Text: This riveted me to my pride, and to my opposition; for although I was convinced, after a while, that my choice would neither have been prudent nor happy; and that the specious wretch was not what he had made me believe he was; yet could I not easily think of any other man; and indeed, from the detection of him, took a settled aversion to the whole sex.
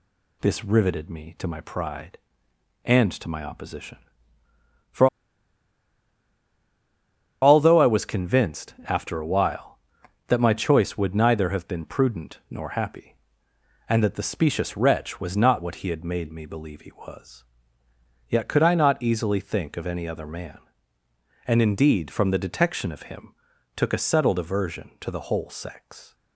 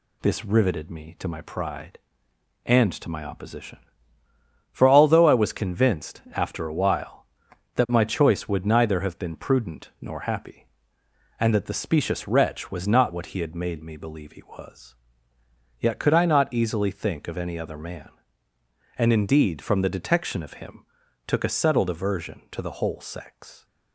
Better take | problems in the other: second | pauses between "for" and "although"; strong; at 5.0 s; 2.3 s long

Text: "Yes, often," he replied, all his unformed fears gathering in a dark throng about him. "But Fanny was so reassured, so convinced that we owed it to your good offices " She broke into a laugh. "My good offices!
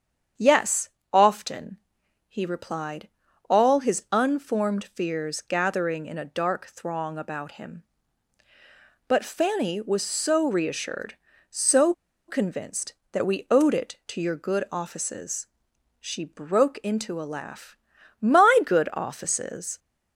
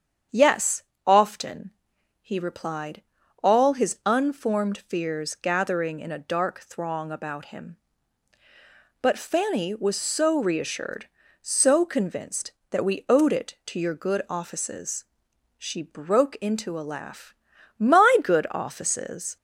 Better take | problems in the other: second | starts louder than the rest; strong; until 1.6 s; 8 dB; strong in the second // pauses between "so" and "convinced"; slight; at 11.9 s; 0.34 s long

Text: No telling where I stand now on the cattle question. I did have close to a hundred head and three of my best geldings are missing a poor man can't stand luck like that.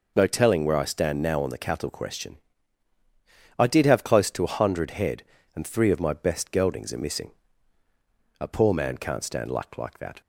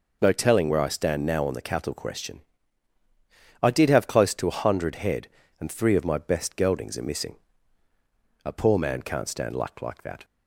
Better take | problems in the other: neither | pauses between "missing" and "a"; the same in both

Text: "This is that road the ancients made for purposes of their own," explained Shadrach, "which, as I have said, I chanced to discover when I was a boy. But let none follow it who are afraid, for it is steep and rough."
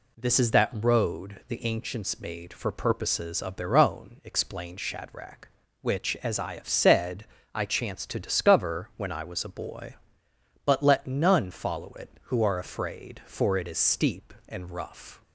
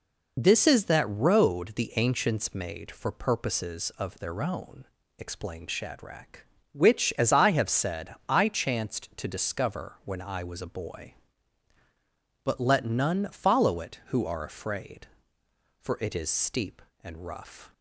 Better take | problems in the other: neither | none

